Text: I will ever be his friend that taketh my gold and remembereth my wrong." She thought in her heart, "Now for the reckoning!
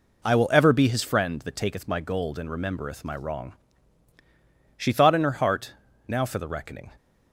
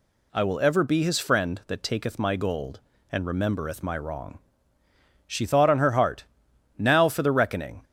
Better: first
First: none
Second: says "on" for "in"; at 5.6 s

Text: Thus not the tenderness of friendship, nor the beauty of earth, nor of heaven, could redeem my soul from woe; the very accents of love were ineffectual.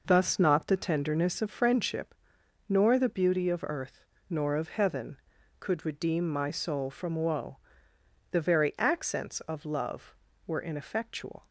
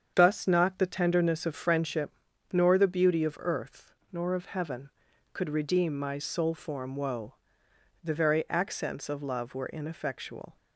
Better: first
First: none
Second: starts louder than the rest; strong; until 1.1 s; 7.5 dB // says "form" for "from"; at 6.5 s

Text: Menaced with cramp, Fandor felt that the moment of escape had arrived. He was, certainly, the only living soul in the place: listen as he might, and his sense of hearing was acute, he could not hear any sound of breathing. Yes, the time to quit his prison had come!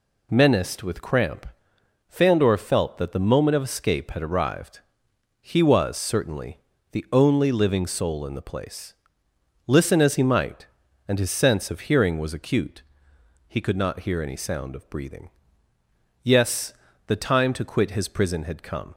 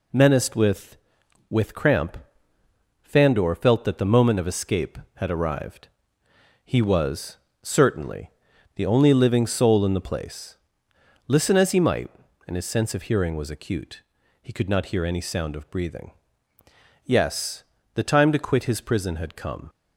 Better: first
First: none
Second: says "with" twice; at 1.5 s

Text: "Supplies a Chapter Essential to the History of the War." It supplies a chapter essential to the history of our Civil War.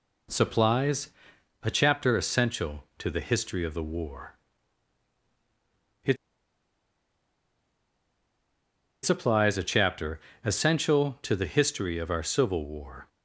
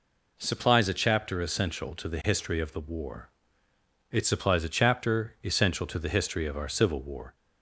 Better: second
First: pauses between "Supplies" and "a"; noticeable; at 1.0 s; 0.54 s long // pauses between "It" and "supplies"; strong; at 6.1 s; 2.8 s long // pauses between "chapter" and "essential"; slight; at 10.1 s; 0.24 s long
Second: none

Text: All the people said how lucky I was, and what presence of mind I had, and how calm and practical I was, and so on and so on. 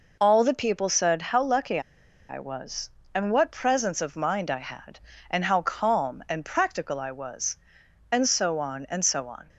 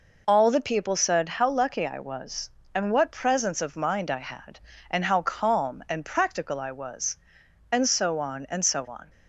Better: second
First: pauses between "lucky" and "I"; noticeable; at 1.7 s; 0.49 s long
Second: none

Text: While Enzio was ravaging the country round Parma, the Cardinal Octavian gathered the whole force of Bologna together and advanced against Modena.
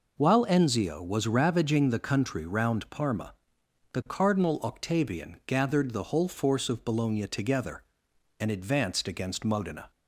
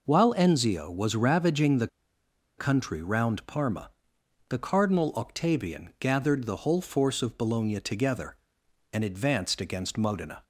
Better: first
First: none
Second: pauses between "the" and "country"; noticeable; at 1.8 s; 0.70 s long

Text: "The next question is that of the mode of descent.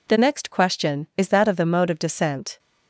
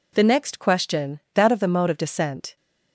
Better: first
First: none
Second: skips "is"; at 1.2 s

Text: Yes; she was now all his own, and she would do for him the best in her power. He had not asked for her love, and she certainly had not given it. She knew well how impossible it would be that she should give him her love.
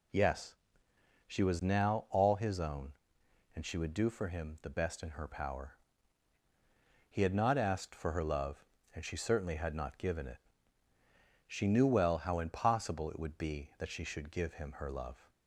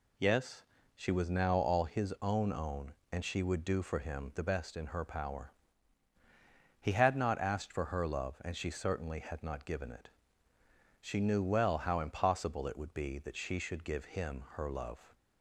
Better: first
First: none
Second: says "own" twice; at 2.5 s

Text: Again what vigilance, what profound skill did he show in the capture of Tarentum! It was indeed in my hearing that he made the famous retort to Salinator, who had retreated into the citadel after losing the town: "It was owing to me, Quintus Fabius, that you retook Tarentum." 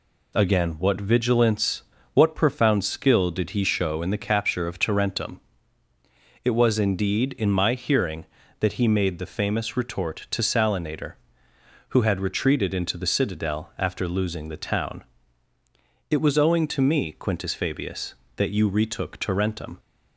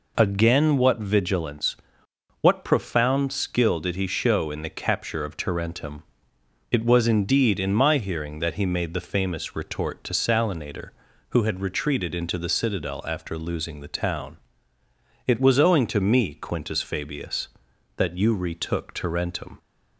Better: neither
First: none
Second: none

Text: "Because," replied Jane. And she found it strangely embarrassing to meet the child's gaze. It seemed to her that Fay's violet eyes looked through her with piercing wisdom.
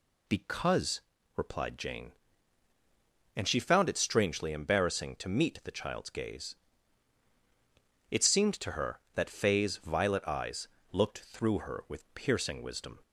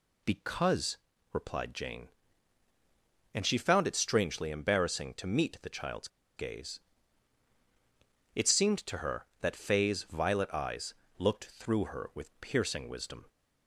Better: first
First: pauses between "eyes" and "looked"; slight; at 10.6 s; 0.24 s long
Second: pauses between "child's" and "gaze"; slight; at 6.0 s; 0.29 s long // pauses between "eyes" and "looked"; slight; at 10.9 s; 0.24 s long

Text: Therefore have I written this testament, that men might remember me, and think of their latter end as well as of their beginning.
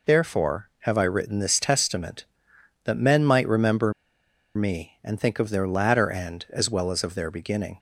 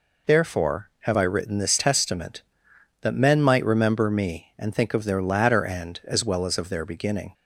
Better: second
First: pauses between "remember" and "me"; noticeable; at 3.9 s; 0.64 s long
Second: none

